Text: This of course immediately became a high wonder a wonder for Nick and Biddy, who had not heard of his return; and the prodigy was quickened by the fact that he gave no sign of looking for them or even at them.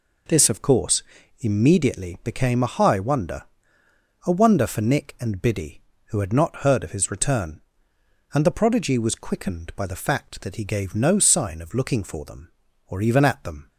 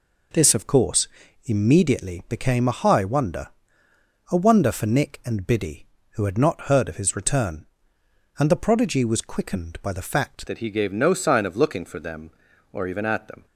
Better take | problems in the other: first | pauses between "course" and "immediately"; slight; at 1.0 s; 0.36 s long; slight in the first // pauses between "wonder" and "a"; noticeable; at 3.4 s; 0.82 s long; noticeable in the first // changes voice at "that"; from 10.4 s on; 3.0 s long

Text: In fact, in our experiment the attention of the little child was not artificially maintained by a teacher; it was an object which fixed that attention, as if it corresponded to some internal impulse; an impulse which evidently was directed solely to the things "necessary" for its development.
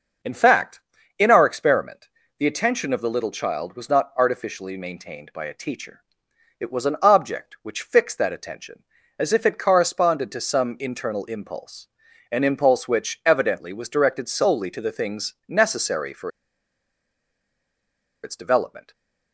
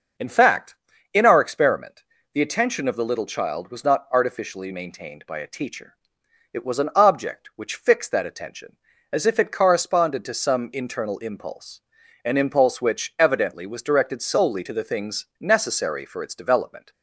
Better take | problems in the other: second | pauses between "experiment" and "the"; slight; at 2.0 s; 0.30 s long; slight in the second // pauses between "for" and "its"; strong; at 16.2 s; 1.9 s long

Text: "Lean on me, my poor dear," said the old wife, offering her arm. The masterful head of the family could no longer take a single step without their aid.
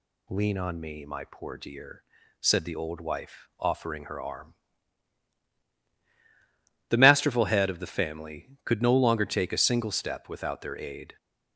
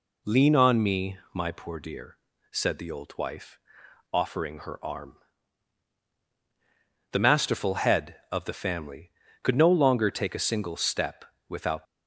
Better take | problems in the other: first | pauses between "step" and "without"; slight; at 11.2 s; 0.24 s long // stops before "their aid"; at 11.8 s

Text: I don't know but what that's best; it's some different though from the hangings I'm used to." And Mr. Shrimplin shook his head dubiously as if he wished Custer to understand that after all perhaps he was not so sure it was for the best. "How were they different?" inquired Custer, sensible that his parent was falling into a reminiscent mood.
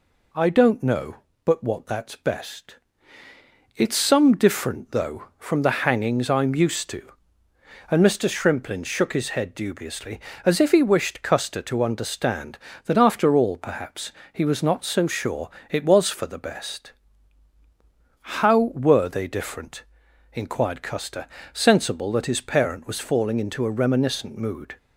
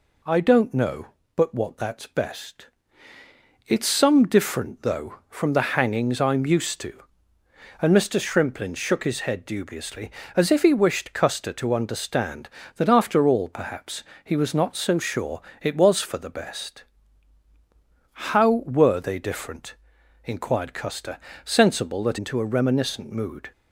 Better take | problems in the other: first | pauses between "perhaps" and "he"; slight; at 14.0 s; 0.18 s long; slight in the first // pauses between "sure" and "it"; slight; at 15.4 s; 0.18 s long; slight in the first // skips "his parent was falling"; at 22.1 s

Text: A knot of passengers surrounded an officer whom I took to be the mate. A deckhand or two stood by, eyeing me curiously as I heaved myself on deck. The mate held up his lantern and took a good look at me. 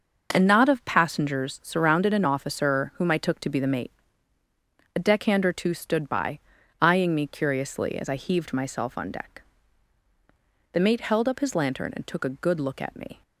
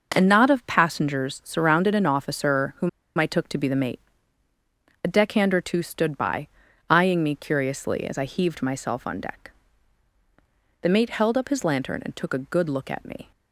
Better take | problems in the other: first | pauses between "whom" and "I"; slight; at 2.8 s; 0.29 s long

